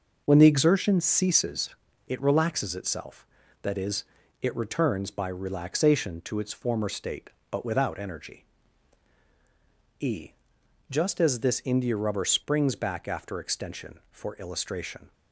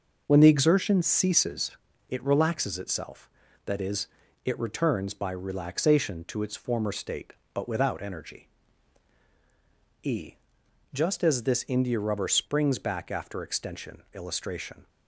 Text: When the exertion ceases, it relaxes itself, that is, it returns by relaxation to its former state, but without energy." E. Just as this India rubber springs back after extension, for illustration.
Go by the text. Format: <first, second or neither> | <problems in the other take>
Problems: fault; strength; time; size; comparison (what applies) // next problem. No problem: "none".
first | skips "for"; at 14.0 s